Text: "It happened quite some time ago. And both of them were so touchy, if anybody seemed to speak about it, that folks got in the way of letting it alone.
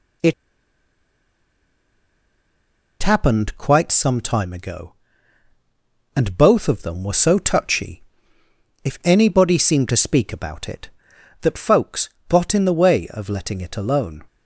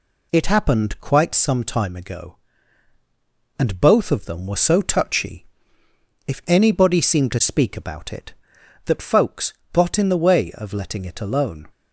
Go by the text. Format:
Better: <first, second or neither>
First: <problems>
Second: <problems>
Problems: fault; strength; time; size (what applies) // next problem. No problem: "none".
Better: second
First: pauses between "It" and "happened"; strong; at 0.3 s; 2.6 s long // pauses between "folks" and "got"; slight; at 12.0 s; 0.20 s long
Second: pauses between "folks" and "got"; slight; at 9.5 s; 0.20 s long